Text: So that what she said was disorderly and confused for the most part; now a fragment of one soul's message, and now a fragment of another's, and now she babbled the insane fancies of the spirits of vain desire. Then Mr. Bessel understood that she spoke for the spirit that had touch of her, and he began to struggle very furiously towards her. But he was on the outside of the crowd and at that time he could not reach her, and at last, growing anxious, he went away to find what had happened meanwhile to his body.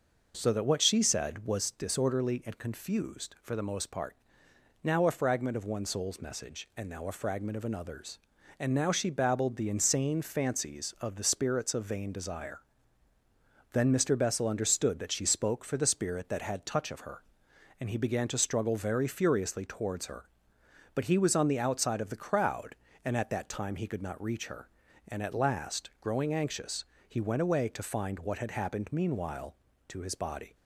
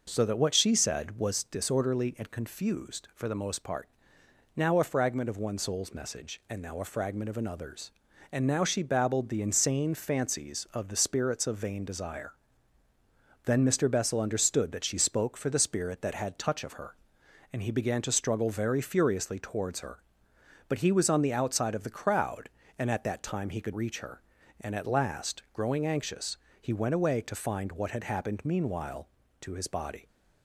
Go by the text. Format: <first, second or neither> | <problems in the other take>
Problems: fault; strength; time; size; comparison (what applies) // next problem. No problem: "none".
first | skips "not"; at 23.7 s